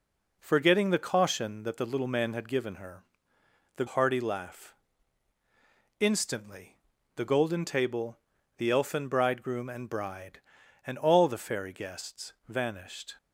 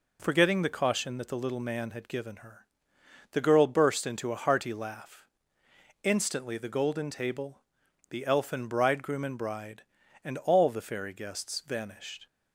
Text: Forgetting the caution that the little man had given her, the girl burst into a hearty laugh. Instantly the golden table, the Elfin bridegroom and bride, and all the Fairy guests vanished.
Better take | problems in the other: second | skips "girl burst into a"; at 3.8 s // pauses between "Instantly" and "the"; at 6.7 s; 0.44 s long

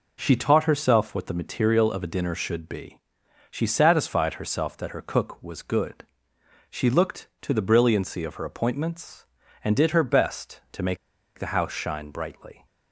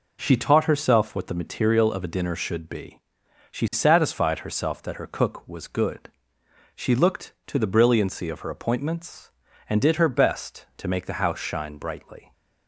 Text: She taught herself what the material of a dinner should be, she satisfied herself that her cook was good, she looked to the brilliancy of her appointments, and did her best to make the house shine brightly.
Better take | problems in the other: second | pauses between "make" and "the"; at 10.9 s; 0.40 s long

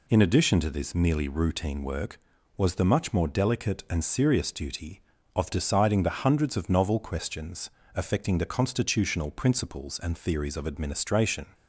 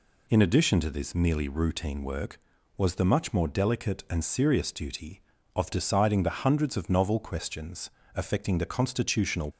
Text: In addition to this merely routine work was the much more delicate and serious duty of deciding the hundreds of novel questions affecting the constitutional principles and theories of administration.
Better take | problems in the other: first | pauses between "questions" and "affecting"; slight; at 7.9 s; 0.24 s long; slight in the first // stops before "principles and theories of administration"; at 9.5 s

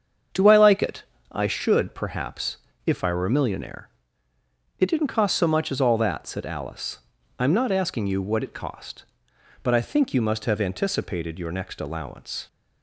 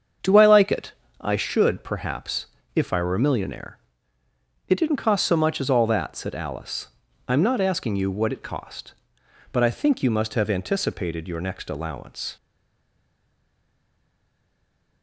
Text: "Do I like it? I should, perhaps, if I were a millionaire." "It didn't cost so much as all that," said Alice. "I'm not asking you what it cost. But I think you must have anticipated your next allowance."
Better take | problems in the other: first | starts louder than the rest; strong; until 1.5 s; 7 dB; strong in the first // stays silent after the last word; strong; from 12.3 s on; 2.7 s long

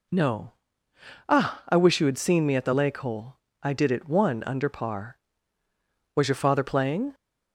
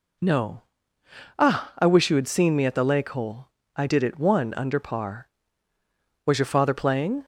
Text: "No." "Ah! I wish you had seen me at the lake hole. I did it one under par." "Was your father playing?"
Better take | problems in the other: neither | none

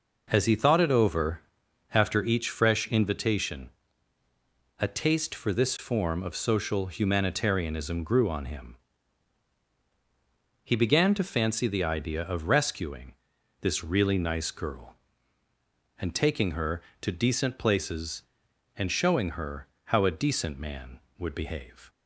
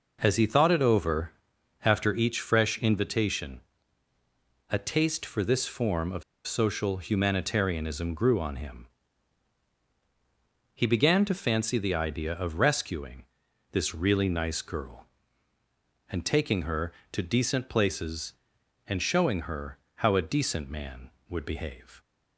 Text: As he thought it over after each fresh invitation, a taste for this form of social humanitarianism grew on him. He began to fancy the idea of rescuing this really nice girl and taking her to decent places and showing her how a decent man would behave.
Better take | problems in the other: first | pauses between "over" and "after"; noticeable; at 1.3 s; 0.54 s long; noticeable in the first // pauses between "of" and "social"; slight; at 6.2 s; 0.23 s long // pauses between "rescuing" and "this"; noticeable; at 13.2 s; 0.46 s long; noticeable in the first // pauses between "her" and "how"; slight; at 19.7 s; 0.20 s long; slight in the first

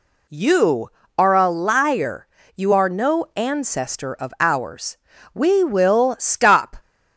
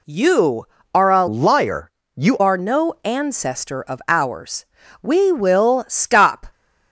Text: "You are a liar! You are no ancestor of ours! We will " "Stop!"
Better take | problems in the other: first | changes voice from "liar" to "You"; from 1.2 to 2.3 s; 1.1 s long

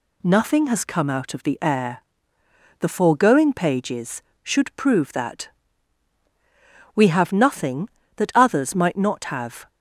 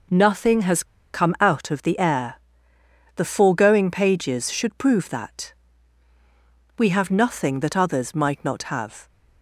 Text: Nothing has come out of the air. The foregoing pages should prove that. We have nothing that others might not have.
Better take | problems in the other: first | pauses between "has" and "come"; slight; at 0.8 s; 0.29 s long

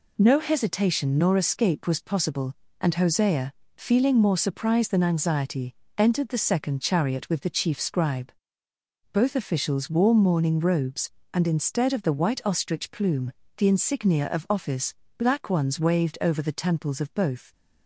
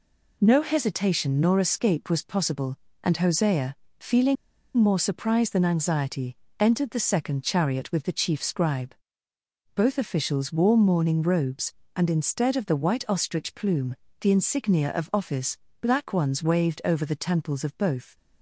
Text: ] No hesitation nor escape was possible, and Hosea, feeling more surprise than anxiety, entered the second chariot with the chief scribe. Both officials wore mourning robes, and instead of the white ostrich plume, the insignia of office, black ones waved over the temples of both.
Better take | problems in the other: first | pauses between "feeling" and "more"; at 4.3 s; 0.41 s long

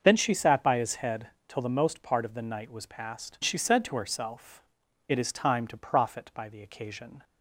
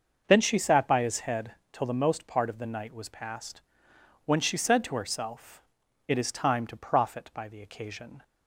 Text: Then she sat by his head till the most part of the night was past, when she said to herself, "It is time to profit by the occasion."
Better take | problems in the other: second | starts louder than the rest; until 1.0 s; 6.5 dB; noticeable in the second // pauses between "head" and "till"; slight; at 1.2 s; 0.20 s long; slight in the second // skips "when"; at 3.3 s

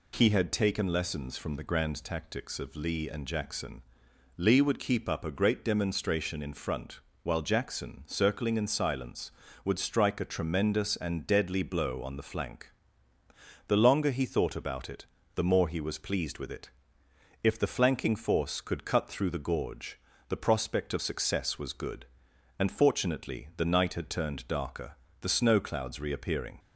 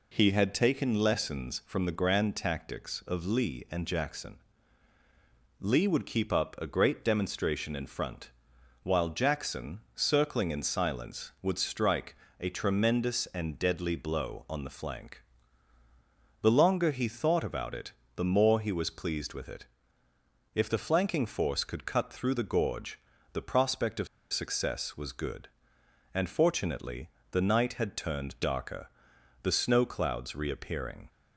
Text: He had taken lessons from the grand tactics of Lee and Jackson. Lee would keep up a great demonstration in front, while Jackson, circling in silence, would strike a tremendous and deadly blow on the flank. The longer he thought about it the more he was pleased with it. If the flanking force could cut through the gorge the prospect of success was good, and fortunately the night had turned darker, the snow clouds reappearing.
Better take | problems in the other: first | pauses between "strike" and "a"; slight; at 12.1 s; 0.24 s long // pauses between "it" and "the"; slight; at 17.9 s; 0.24 s long; slight in the first // pauses between "gorge" and "the"; slight; at 22.9 s; 0.34 s long; slight in the first // pauses between "of" and "success"; slight; at 24.0 s; 0.26 s long // pauses between "fortunately" and "the"; slight; at 27.0 s; 0.24 s long

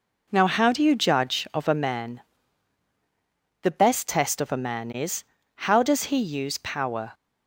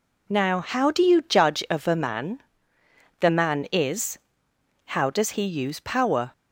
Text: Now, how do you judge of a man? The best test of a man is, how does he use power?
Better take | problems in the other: first | skips "best test of a"; at 3.2 s

